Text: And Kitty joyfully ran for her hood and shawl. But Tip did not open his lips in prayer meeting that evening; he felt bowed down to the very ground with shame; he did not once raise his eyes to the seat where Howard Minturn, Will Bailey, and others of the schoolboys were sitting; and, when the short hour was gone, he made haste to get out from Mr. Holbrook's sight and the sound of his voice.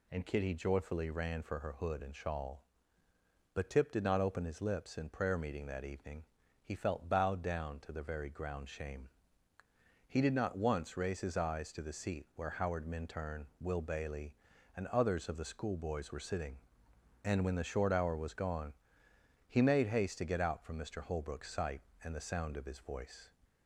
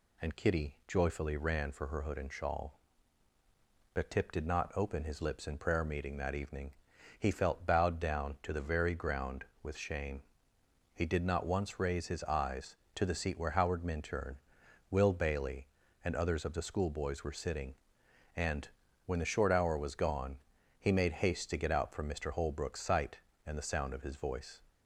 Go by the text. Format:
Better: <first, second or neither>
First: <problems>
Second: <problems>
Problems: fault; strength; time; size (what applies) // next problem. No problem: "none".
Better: second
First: skips "with"; at 8.6 s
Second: none